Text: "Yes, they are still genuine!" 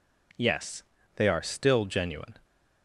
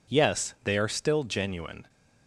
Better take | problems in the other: neither | none

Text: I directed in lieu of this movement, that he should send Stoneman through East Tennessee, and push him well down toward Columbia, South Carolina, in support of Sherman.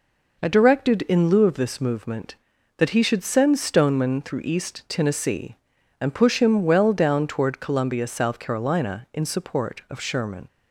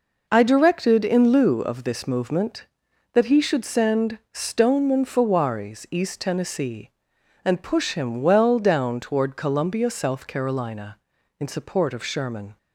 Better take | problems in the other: first | pauses between "send" and "Stoneman"; slight; at 4.1 s; 0.16 s long // says "fawaris" for "through"; at 5.0 s

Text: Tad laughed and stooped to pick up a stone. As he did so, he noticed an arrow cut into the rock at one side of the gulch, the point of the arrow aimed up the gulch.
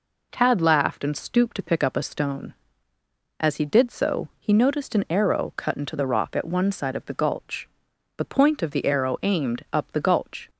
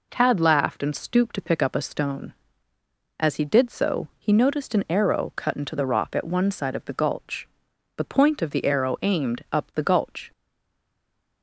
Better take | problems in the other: first | stays silent after the last word; from 10.3 s on; 1.1 s long

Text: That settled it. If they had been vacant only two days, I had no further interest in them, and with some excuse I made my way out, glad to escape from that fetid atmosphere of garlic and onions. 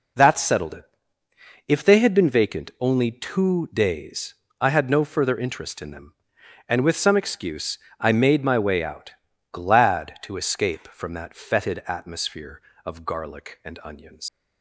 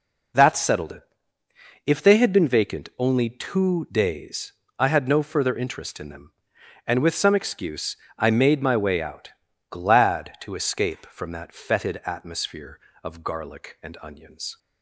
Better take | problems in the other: second | pauses between "excuse" and "I"; slight; at 7.7 s; 0.22 s long; slight in the second // leaves "onions" unfinished; at 14.2 s; 115 ms

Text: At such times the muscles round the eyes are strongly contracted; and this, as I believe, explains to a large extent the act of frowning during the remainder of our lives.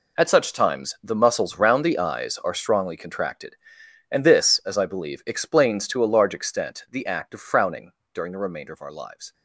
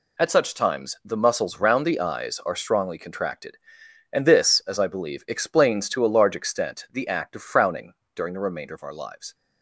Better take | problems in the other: second | gets quieter; strong; throughout; 12.5 dB // pauses between "frowning" and "during"; slight; at 7.9 s; 0.20 s long; slight in the second

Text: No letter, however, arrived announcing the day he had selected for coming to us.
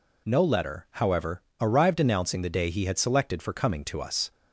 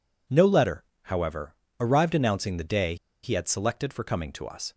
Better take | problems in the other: first | pauses between "day" and "he"; slight; at 2.9 s; 0.28 s long

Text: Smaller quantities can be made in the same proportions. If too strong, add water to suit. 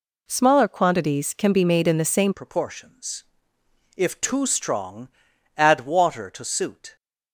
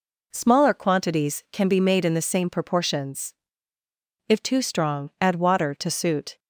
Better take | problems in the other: second | changes voice at "proportions"; from 2.3 s on; 4.6 s long

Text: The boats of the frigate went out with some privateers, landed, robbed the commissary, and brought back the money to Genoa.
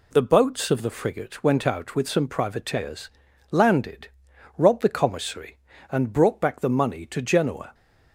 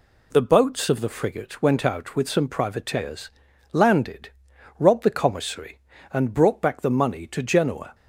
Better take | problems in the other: neither | none

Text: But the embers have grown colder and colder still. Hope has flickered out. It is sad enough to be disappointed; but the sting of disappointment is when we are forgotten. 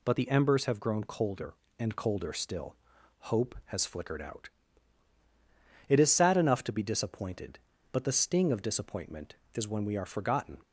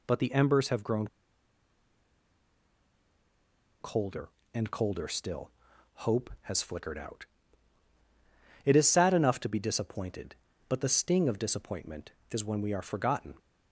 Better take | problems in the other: first | pauses between "grown" and "colder"; strong; at 1.0 s; 2.7 s long

